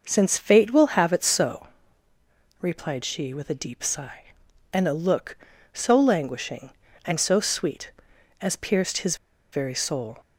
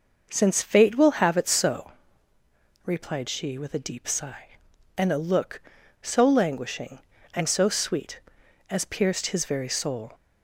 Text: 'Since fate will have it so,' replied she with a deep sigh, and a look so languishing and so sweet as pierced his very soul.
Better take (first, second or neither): second